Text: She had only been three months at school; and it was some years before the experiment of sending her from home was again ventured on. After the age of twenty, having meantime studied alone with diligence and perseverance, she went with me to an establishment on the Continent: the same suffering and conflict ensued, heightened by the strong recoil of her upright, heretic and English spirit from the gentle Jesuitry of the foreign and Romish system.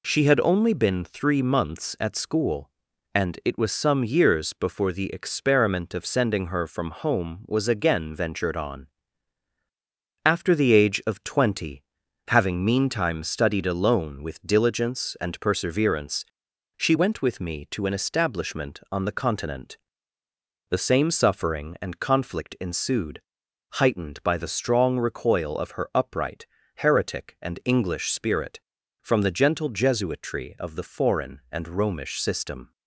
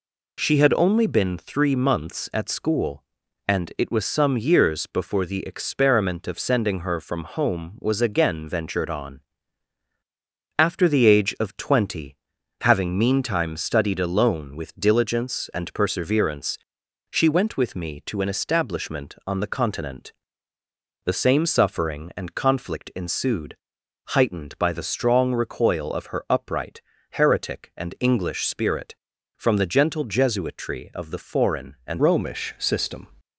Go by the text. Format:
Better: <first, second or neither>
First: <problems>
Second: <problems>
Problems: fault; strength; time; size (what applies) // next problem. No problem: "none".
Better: first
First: none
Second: changes voice at "Romish"; from 31.9 s on; 1.1 s long